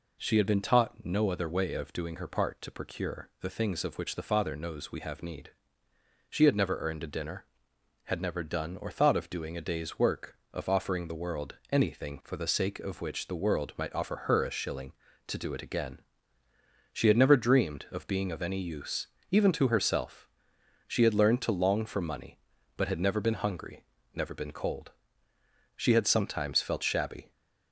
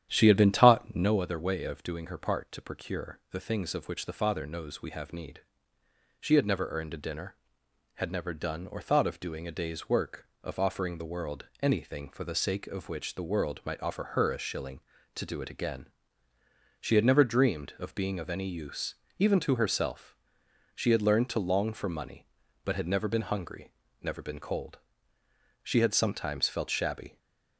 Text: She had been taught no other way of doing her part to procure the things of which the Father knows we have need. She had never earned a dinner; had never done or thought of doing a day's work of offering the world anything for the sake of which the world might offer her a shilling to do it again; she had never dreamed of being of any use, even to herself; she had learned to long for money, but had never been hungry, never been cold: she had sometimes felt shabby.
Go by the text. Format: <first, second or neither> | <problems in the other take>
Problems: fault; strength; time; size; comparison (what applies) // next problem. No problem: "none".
first | starts louder than the rest; strong; until 1.3 s; 10 dB // pauses between "world" and "anything"; slight; at 11.4 s; 0.16 s long; slight in the first // stays silent after the last word; slight; from 27.0 s on; 0.5 s long